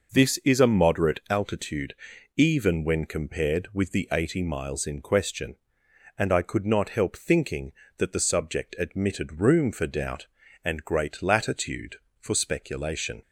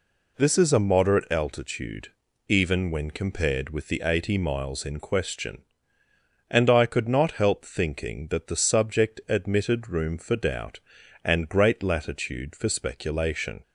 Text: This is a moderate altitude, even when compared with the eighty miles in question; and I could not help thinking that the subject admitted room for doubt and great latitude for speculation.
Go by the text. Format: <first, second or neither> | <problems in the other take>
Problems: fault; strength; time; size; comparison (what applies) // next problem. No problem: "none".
neither | none